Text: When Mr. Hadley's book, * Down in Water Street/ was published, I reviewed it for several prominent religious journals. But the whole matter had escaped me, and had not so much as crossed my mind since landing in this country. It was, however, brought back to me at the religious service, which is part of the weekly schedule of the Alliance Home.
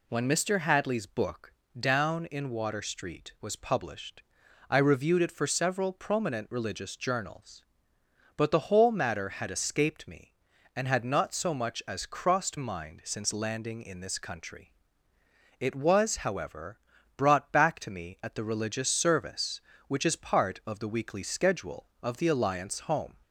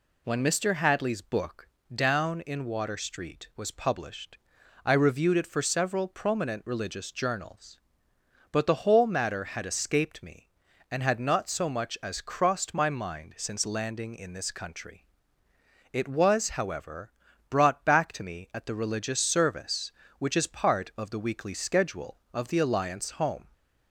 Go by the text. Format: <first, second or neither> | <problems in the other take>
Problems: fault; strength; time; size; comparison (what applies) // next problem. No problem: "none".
second | skips "my"; at 12.5 s